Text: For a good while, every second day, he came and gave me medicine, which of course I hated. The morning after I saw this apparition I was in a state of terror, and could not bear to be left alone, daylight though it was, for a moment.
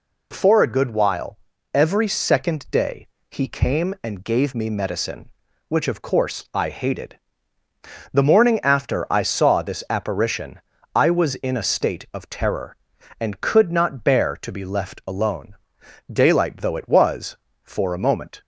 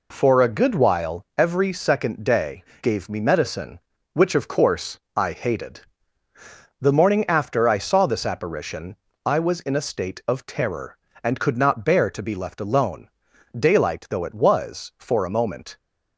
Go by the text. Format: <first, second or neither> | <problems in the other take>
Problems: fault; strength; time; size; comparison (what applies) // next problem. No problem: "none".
first | skips "he came and"; at 2.7 s // pauses between "course" and "I"; slight; at 4.9 s; 0.16 s long // pauses between "apparition" and "I"; slight; at 8.9 s; 0.28 s long; slight in the first